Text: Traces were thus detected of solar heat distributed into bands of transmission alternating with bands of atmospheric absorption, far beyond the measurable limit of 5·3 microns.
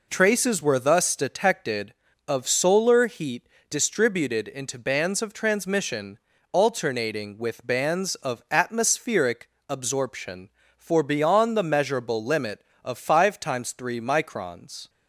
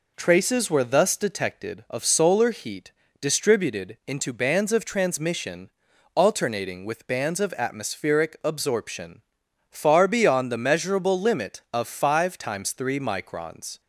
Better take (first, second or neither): second